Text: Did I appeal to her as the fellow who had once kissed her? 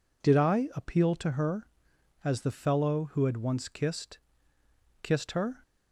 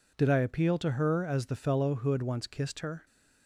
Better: second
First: says "kissed" twice; at 5.0 s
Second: none

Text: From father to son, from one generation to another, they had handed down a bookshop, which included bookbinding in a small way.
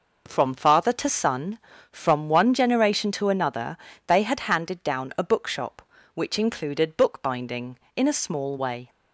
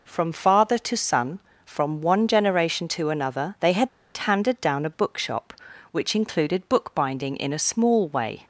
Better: first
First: none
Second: pauses between "had" and "handed"; slight; at 3.8 s; 0.27 s long

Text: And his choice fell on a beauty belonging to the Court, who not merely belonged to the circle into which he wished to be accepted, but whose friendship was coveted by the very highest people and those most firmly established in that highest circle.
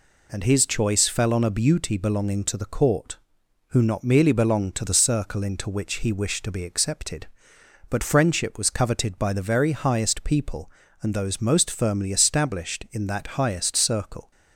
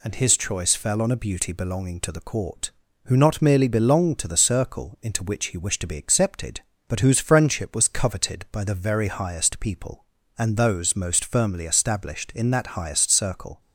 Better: second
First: skips "whose"; at 8.0 s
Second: none

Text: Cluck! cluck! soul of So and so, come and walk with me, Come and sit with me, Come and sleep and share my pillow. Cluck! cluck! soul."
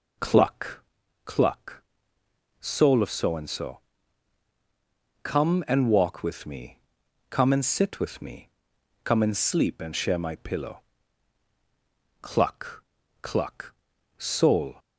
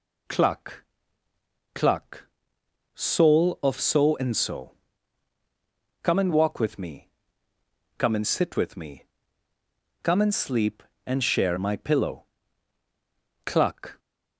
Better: first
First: none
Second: stops before "cluck soul"; at 13.9 s

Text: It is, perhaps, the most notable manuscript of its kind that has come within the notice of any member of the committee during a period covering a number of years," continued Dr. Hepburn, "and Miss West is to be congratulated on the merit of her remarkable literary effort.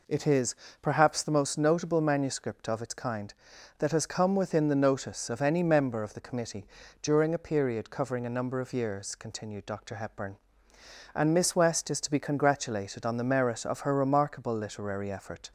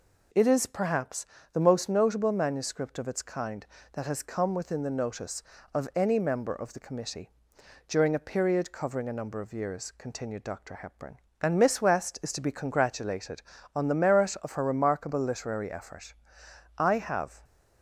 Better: first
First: pauses between "committee" and "during"; slight; at 6.6 s; 0.36 s long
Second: pauses between "committee" and "during"; noticeable; at 7.2 s; 0.58 s long // goes on to say "I have"; noticeable; from 16.7 s on; 0.64 s long

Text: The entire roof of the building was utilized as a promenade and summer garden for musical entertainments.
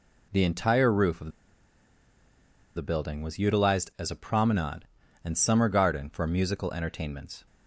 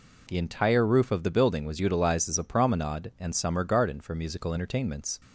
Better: second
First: pauses between "of" and "the"; strong; at 1.3 s; 1.4 s long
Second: none

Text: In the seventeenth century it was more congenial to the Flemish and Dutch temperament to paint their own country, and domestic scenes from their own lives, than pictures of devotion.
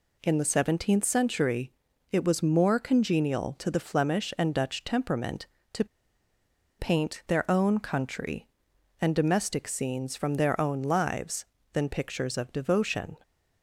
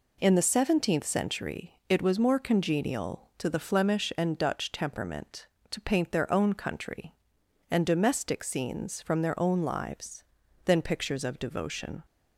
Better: second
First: pauses between "century" and "it"; at 1.7 s; 0.40 s long // pauses between "to" and "paint"; noticeable; at 5.8 s; 0.94 s long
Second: none

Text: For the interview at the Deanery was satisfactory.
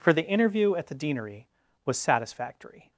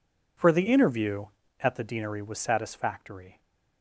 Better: neither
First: none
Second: none

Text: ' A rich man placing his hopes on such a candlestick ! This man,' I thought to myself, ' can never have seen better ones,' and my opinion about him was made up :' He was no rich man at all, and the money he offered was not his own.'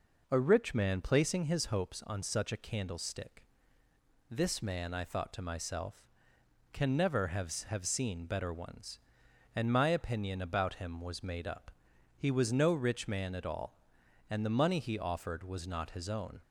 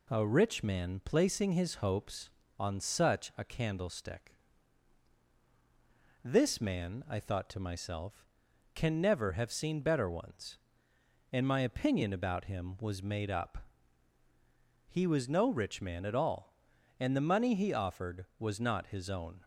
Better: second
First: says "have" twice; at 7.6 s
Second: none

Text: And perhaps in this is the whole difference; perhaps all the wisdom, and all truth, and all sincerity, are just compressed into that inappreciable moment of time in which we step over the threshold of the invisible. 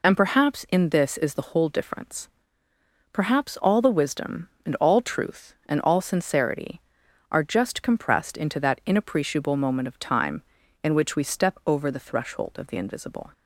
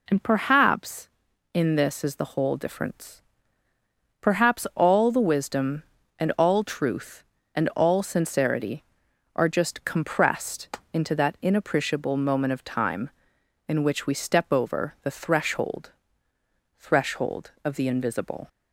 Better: first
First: none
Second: pauses between "compressed" and "into"; slight; at 10.7 s; 0.16 s long // says "threshold" twice; at 16.7 s

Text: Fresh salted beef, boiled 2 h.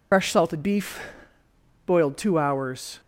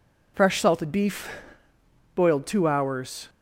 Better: second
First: loses the start of "Fresh"; at 0.1 s; 55 ms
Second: none

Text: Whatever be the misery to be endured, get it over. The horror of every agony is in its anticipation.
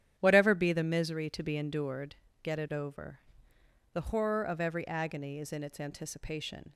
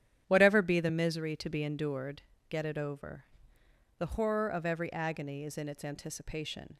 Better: neither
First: starts louder than the rest; strong; until 1.1 s; 10.5 dB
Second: starts louder than the rest; strong; until 1.2 s; 10.5 dB

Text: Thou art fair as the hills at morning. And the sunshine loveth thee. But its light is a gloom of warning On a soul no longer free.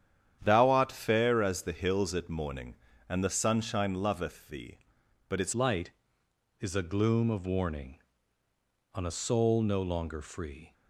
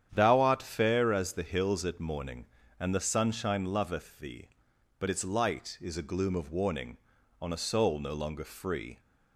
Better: second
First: starts louder than the rest; strong; until 1.4 s; 9 dB // changes voice at "light"; from 5.5 s on; 5.2 s long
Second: starts louder than the rest; strong; until 1.1 s; 9 dB

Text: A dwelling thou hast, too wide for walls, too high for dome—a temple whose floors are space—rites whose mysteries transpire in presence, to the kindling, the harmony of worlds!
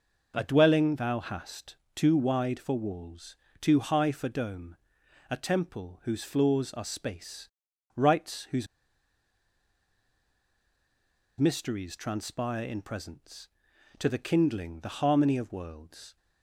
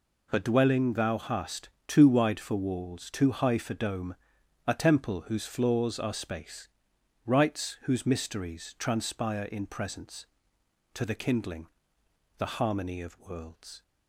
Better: second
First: pauses between "whose" and "mysteries"; strong; at 8.6 s; 2.7 s long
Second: none

